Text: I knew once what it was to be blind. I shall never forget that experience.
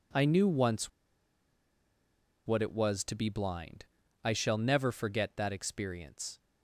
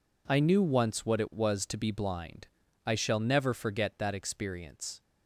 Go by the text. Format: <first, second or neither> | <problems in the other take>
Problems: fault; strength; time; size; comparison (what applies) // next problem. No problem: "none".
second | pauses between "once" and "what"; strong; at 0.8 s; 1.5 s long